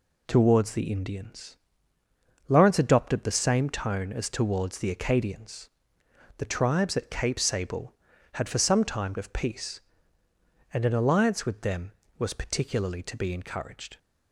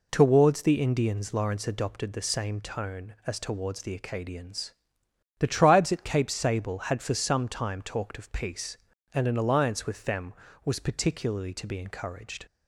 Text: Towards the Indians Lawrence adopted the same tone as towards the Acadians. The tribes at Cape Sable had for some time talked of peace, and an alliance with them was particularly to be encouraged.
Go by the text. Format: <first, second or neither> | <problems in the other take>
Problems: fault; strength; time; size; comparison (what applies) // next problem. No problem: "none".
second | pauses between "Indians" and "Lawrence"; noticeable; at 1.5 s; 0.92 s long // skips "talked"; at 9.1 s